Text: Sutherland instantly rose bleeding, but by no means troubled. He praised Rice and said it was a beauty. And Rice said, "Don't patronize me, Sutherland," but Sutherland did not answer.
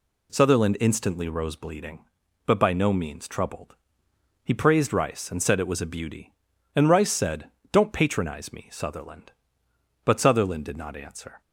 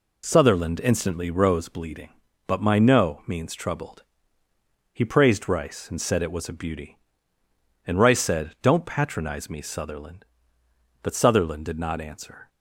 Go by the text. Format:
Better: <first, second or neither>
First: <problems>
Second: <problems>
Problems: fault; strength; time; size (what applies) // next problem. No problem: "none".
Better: first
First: none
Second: says "my" for "by"; at 2.5 s